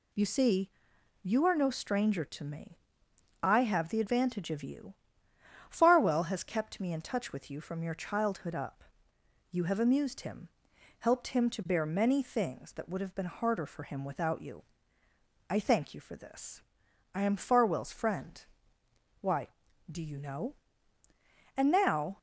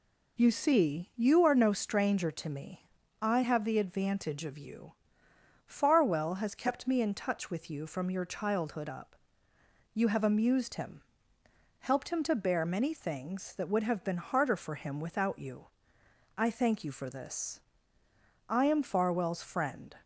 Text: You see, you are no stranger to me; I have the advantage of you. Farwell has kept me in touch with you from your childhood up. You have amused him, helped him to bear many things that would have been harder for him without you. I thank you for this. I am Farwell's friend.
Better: second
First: goes on to say "Why do you know and now"; strong; from 19.1 s on; 2.9 s long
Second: none

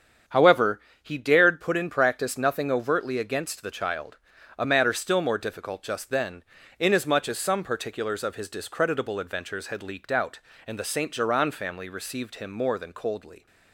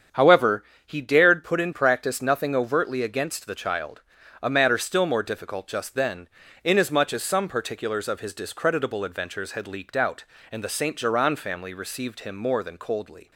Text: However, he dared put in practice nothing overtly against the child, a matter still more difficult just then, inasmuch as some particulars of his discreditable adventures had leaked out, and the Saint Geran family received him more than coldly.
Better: neither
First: starts louder than the rest; strong; until 1.5 s; 8 dB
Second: starts louder than the rest; strong; until 1.3 s; 8 dB

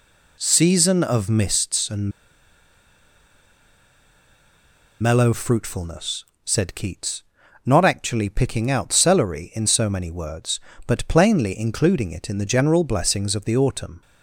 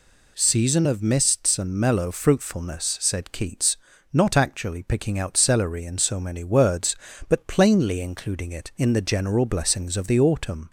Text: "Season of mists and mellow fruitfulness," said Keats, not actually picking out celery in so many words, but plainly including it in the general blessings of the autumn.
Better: second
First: pauses between "and" and "mellow"; strong; at 2.1 s; 2.9 s long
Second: none

